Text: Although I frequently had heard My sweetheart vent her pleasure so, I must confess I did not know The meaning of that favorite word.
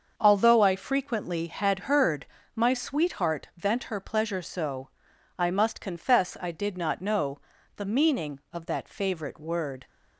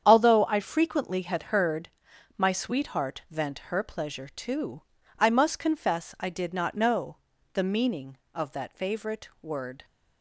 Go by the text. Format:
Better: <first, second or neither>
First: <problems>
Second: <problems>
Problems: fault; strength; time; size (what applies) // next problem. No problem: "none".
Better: first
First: starts louder than the rest; until 1.1 s; 6.5 dB // pauses between "heard" and "My"; slight; at 2.2 s; 0.30 s long // pauses between "know" and "The"; slight; at 7.3 s; 0.36 s long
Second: starts louder than the rest; strong; until 1.0 s; 8 dB // pauses between "heard" and "My"; noticeable; at 1.8 s; 0.48 s long // says "too" for "so"; at 4.2 s // pauses between "know" and "The"; slight; at 7.1 s; 0.34 s long